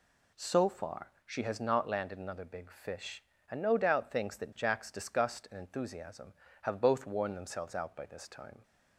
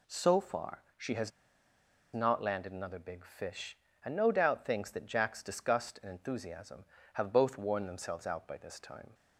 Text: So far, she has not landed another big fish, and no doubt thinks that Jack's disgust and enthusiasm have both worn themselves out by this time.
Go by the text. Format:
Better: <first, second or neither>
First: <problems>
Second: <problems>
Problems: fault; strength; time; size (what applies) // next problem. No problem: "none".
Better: first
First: none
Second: pauses between "has" and "not"; noticeable; at 1.3 s; 0.84 s long